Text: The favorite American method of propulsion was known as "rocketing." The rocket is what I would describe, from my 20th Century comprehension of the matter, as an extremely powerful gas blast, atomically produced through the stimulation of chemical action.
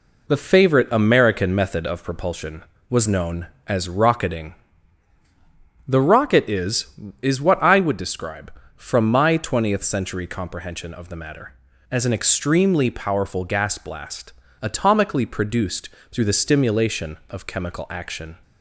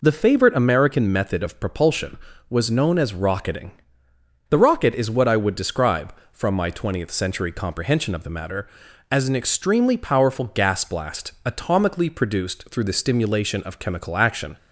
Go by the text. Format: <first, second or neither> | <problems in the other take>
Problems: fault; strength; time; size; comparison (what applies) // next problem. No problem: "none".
second | says "is" twice; at 7.2 s // pauses between "produced" and "through"; slight; at 15.8 s; 0.22 s long